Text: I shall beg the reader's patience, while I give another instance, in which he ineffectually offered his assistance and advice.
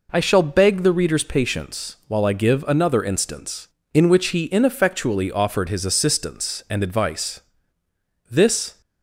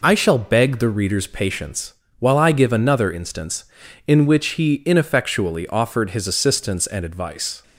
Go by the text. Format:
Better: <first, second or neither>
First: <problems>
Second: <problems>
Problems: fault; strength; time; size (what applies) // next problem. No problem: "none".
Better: second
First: goes on to say "This"; from 8.3 s on; 0.50 s long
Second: none